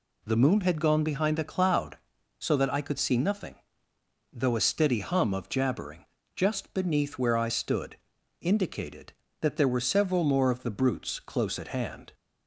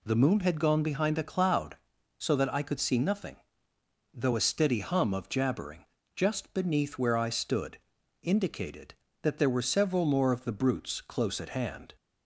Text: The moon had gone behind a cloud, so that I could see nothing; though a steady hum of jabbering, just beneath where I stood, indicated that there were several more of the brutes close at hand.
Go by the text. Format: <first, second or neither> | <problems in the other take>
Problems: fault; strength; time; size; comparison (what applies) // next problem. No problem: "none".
neither | none